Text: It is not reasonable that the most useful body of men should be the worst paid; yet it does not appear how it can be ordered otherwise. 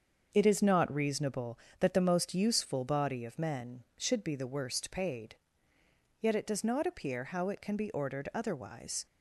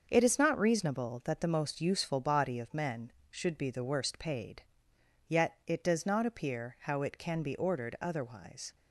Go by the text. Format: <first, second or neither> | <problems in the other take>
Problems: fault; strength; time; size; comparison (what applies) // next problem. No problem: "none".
neither | starts louder than the rest; the same in both